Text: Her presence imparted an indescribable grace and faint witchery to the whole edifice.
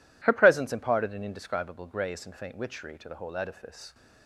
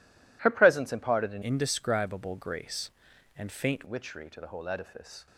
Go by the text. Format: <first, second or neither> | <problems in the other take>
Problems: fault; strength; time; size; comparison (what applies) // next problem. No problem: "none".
first | changes voice from "indescribable" to "faint"; from 1.4 to 3.8 s; 2.4 s long